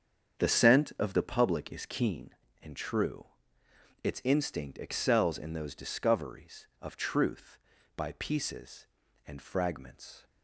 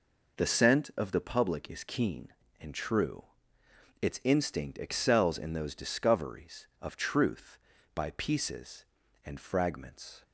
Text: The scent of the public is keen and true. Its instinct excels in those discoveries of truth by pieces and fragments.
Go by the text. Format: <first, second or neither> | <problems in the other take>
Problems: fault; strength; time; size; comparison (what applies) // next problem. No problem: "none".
second | starts louder than the rest; strong; until 2.3 s; 7.5 dB